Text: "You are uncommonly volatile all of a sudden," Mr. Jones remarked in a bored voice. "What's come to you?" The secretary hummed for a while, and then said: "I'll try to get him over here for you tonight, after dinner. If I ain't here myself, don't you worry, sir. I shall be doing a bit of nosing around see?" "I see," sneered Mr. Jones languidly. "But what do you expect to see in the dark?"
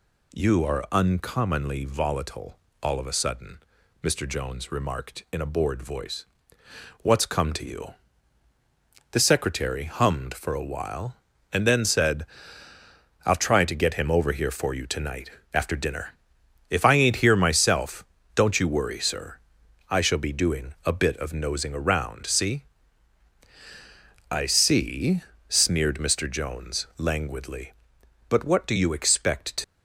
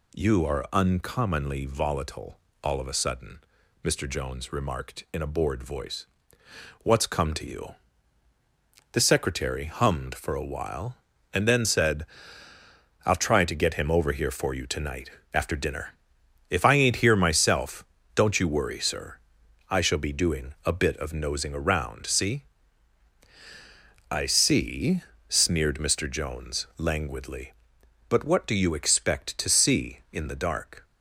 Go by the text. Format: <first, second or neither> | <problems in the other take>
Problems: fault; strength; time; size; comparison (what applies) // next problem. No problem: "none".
second | pauses between "volatile" and "all"; slight; at 2.5 s; 0.24 s long; slight in the second // stops before "see in the dark"; at 29.6 s